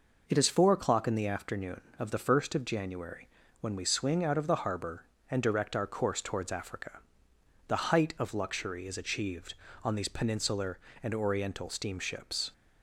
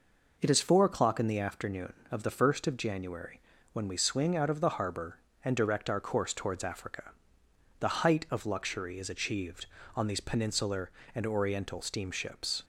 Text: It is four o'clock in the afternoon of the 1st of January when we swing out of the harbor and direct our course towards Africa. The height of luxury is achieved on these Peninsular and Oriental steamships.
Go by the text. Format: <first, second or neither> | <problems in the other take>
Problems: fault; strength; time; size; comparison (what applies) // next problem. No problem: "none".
neither | pauses between "January" and "when"; slight; the same in both